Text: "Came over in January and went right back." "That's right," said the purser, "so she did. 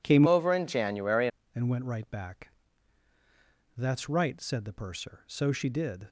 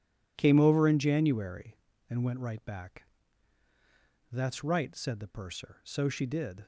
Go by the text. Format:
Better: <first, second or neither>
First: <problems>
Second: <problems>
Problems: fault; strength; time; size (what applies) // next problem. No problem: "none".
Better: second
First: changes voice from "over" to "January"; from 0.2 to 1.2 s; 1.0 s long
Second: none